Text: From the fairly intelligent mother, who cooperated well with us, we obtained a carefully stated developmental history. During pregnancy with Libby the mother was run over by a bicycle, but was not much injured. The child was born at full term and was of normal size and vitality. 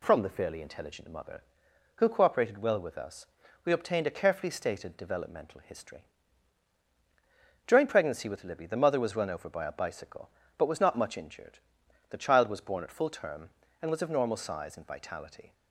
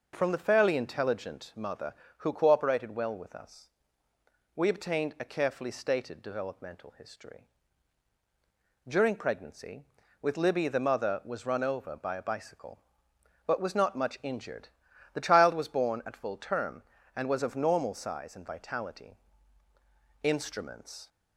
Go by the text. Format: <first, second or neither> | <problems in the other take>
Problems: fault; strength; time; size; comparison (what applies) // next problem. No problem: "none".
first | goes on to say "Instruments"; noticeable; from 20.2 s on; 0.86 s long